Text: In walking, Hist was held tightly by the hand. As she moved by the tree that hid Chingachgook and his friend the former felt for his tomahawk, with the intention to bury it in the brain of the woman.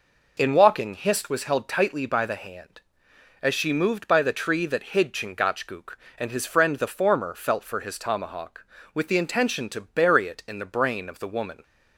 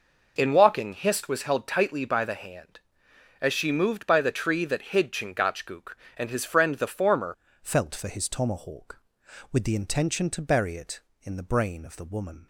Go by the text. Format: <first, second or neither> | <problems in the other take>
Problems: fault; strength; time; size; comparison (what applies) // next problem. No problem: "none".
first | changes voice at "felt"; from 7.6 s on; 4.8 s long